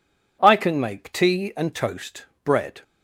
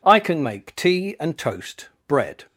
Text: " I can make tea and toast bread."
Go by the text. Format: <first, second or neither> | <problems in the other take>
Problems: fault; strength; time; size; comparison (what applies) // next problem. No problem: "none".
neither | pauses between "toast" and "bread"; slight; the same in both